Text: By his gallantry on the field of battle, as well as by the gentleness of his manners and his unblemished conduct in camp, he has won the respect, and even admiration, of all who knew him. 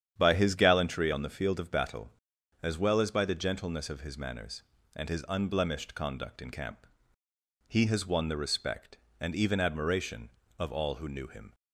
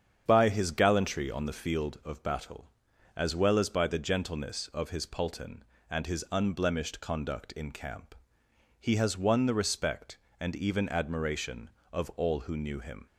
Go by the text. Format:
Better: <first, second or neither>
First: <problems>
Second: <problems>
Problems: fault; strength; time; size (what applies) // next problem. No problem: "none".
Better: first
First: starts louder than the rest; strong; until 1.1 s; 9 dB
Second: starts louder than the rest; strong; until 1.2 s; 8 dB // says "pulton" for "manners"; at 5.0 s